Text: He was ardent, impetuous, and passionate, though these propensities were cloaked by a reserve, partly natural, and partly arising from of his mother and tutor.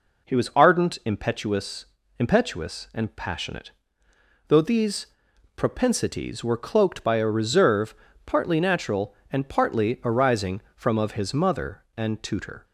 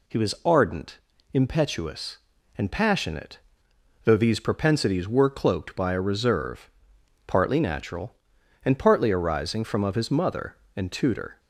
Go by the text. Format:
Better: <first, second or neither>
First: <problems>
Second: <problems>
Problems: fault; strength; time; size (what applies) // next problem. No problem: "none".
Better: second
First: says "impetuous" twice; at 2.1 s // pauses between "these" and "propensities"; noticeable; at 5.0 s; 0.50 s long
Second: none